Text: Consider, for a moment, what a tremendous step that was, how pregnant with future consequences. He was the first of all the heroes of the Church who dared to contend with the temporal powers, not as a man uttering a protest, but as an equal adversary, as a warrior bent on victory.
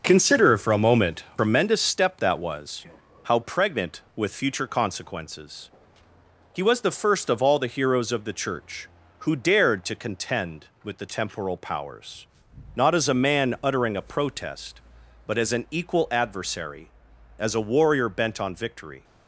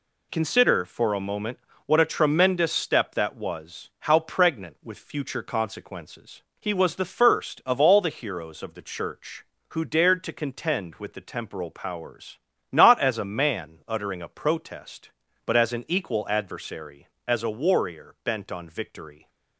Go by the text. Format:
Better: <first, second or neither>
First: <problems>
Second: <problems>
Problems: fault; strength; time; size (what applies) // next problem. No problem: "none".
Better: second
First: skips "what a"; at 1.3 s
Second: none